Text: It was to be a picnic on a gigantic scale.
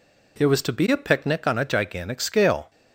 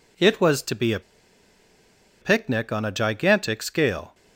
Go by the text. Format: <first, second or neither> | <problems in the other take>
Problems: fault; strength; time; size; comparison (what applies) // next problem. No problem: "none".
first | pauses between "a" and "picnic"; at 1.0 s; 1.2 s long